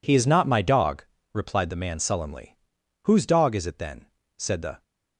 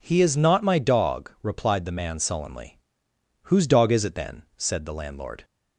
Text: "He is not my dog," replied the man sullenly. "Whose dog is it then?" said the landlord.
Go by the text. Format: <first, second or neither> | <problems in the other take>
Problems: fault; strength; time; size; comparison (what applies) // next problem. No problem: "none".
second | stops before "landlord"; at 4.8 s